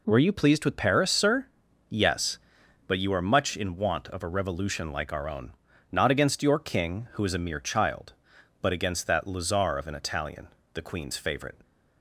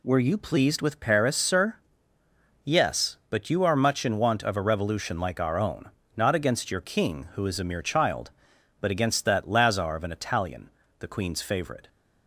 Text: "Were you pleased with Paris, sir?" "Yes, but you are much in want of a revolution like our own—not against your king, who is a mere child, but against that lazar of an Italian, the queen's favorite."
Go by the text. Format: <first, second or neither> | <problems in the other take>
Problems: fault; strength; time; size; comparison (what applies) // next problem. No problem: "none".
neither | none